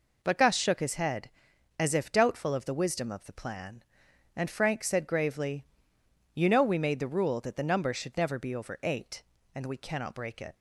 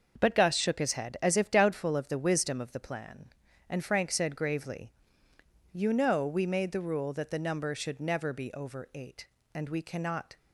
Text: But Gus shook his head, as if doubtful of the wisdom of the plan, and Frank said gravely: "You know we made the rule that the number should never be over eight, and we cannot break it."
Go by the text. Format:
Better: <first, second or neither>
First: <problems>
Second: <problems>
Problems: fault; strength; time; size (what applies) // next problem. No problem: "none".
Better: first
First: none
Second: starts louder than the rest; noticeable; until 1.2 s; 6 dB // stops before "break it"; at 10.3 s